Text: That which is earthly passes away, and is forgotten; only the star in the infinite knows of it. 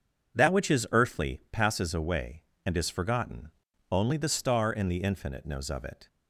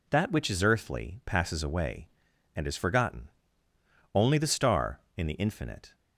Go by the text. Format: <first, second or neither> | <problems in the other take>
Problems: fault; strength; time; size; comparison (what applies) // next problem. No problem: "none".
first | stops before "knows of it"; at 5.9 s